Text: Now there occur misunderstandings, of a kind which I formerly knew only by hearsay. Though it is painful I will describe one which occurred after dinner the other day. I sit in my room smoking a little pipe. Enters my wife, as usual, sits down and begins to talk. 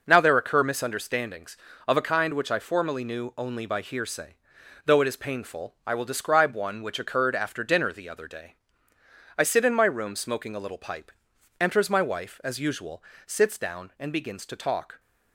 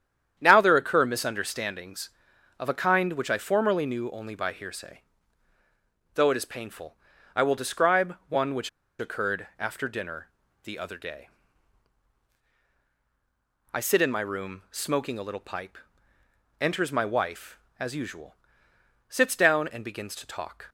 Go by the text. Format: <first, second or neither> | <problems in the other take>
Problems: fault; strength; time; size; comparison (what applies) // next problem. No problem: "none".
first | starts louder than the rest; strong; until 1.3 s; 9 dB // pauses between "painful" and "I"; at 6.9 s; 0.40 s long // pauses between "which" and "occurred"; slight; at 8.6 s; 0.31 s long // pauses between "dinner" and "the"; slight; at 10.2 s; 0.34 s long